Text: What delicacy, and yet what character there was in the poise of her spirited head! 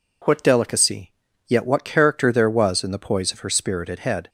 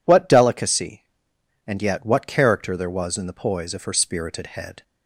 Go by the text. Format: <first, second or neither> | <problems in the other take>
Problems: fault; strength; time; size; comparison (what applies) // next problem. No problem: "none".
second | skips "and"; at 1.2 s